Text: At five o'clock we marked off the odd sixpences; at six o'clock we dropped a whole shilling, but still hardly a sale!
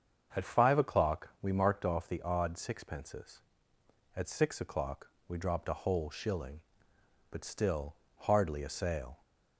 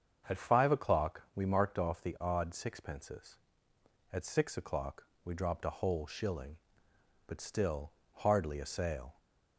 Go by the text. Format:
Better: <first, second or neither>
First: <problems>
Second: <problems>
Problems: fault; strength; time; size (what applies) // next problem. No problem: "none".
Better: neither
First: starts louder than the rest; until 1.4 s; 7 dB // pauses between "o'clock" and "we"; slight; at 5.0 s; 0.18 s long // pauses between "still" and "hardly"; slight; at 7.9 s; 0.18 s long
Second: starts louder than the rest; until 1.3 s; 7 dB // pauses between "o'clock" and "we"; slight; at 5.0 s; 0.18 s long // pauses between "still" and "hardly"; slight; at 7.9 s; 0.18 s long